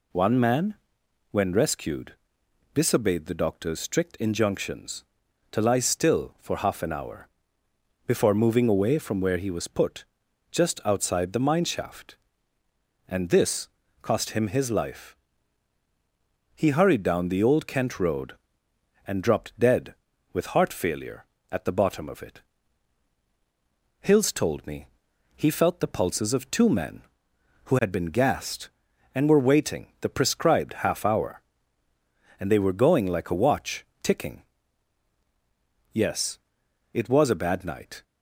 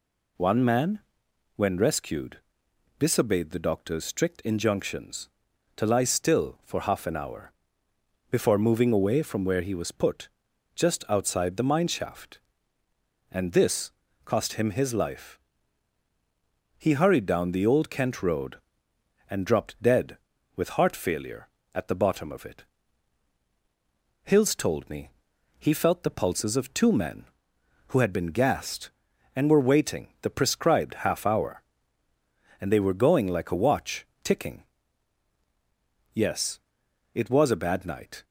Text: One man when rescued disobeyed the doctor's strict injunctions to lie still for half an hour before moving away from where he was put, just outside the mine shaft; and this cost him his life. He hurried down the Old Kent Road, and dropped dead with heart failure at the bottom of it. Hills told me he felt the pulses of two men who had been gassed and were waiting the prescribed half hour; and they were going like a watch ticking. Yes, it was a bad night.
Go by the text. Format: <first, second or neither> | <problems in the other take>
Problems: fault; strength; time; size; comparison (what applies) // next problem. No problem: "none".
neither | pauses between "man" and "when"; noticeable; the same in both // pauses between "rescued" and "disobeyed"; noticeable; the same in both // pauses between "hour" and "before"; noticeable; the same in both // pauses between "this" and "cost"; slight; the same in both // pauses between "me" and "he"; noticeable; the same in both // pauses between "watch" and "ticking"; slight; the same in both